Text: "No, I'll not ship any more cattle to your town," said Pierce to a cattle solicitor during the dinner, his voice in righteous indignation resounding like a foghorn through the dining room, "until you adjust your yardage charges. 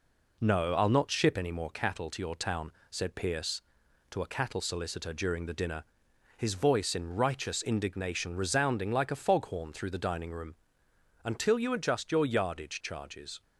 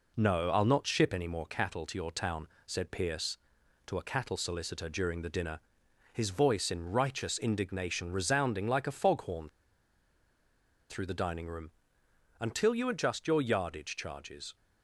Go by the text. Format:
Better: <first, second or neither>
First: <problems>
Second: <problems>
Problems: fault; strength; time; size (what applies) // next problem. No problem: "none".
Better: first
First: none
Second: pauses between "foghorn" and "through"; strong; at 9.4 s; 1.4 s long